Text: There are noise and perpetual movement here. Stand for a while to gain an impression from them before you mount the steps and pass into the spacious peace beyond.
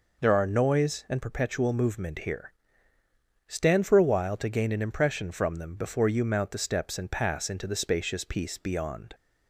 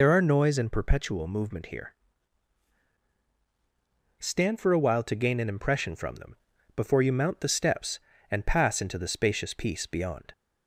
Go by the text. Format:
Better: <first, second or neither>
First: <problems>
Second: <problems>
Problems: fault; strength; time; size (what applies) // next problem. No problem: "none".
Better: first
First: none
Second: loses the start of "There"; at 0.0 s; 65 ms // pauses between "them" and "before"; at 6.3 s; 0.40 s long